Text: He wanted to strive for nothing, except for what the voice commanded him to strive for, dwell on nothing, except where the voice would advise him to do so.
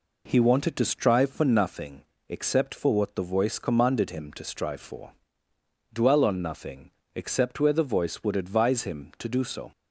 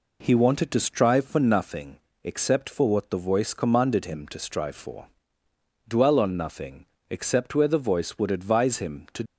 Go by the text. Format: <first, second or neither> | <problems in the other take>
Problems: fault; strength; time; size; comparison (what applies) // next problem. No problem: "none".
first | stops before "do so"; at 9.2 s